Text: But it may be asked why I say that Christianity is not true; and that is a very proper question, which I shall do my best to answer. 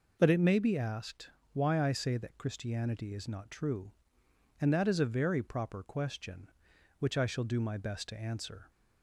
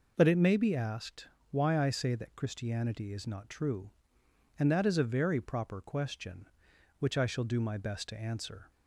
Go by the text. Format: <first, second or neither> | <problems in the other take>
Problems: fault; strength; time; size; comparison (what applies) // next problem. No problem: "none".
neither | pauses between "asked" and "why"; slight; the same in both